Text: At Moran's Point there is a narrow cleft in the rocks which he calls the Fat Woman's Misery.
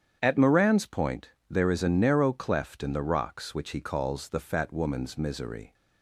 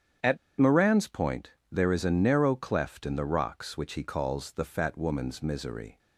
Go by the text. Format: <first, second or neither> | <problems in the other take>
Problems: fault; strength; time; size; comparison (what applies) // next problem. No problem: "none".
first | starts louder than the rest; strong; until 1.4 s; 8.5 dB; strong in the first // pauses between "At" and "Moran's"; slight; at 0.3 s; 0.22 s long // pauses between "Point" and "there"; slight; at 1.5 s; 0.22 s long; slight in the first